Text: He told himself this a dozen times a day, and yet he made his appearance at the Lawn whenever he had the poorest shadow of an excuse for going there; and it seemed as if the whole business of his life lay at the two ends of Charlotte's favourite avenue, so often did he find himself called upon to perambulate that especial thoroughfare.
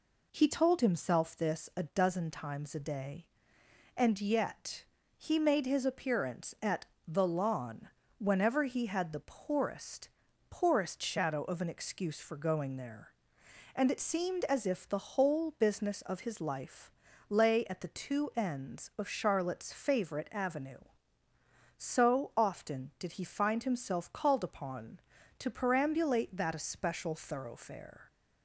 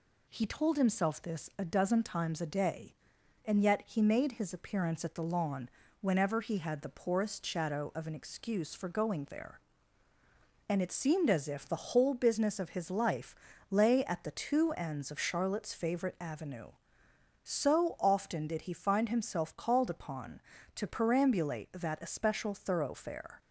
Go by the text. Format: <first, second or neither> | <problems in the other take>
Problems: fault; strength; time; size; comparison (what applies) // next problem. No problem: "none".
second | pauses between "yet" and "he"; slight; at 4.8 s; 0.34 s long // pauses between "at" and "the"; slight; at 6.8 s; 0.22 s long // pauses between "Lawn" and "whenever"; slight; at 7.8 s; 0.32 s long; slight in the second // says "poorest" twice; at 10.5 s // pauses between "life" and "lay"; slight; at 16.9 s; 0.36 s long; slight in the second